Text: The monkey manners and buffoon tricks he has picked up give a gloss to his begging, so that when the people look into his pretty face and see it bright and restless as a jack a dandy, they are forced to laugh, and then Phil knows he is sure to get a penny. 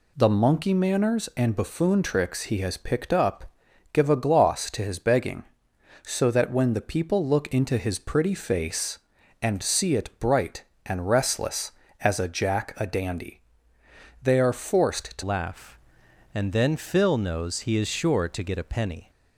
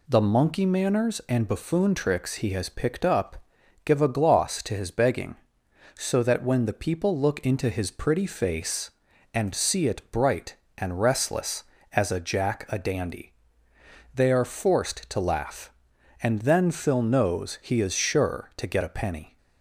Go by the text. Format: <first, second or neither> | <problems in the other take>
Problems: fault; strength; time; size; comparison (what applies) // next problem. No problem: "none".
second | pauses between "up" and "give"; at 3.5 s; 0.40 s long; also in the second // changes voice at "laugh"; from 15.2 s on; 3.8 s long